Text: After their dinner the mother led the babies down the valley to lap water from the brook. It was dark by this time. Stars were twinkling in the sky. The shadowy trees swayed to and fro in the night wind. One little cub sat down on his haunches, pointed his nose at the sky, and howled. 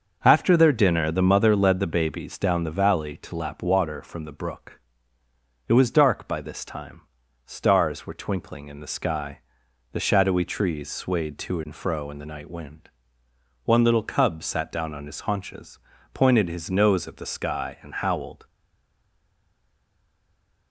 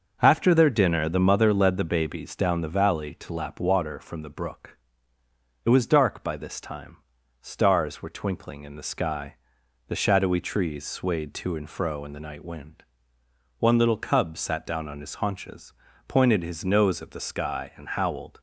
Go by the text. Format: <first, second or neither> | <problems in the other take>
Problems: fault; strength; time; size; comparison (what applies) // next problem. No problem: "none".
second | stays silent after the last word; from 18.4 s on; 2.3 s long